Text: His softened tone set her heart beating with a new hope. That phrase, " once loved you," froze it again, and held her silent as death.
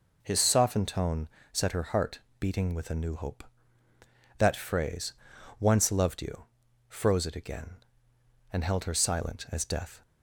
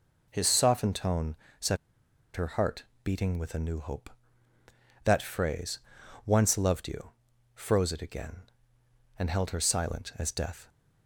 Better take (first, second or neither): first